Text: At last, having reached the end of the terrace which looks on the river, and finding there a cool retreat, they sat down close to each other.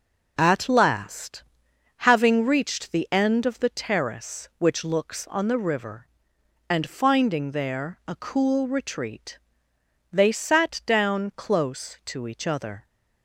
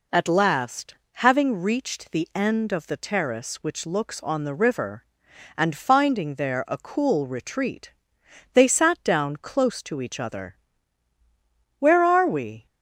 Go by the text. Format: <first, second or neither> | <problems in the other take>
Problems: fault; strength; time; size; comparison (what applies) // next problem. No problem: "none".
first | goes on to say "Where are we"; noticeable; from 11.7 s on; 0.88 s long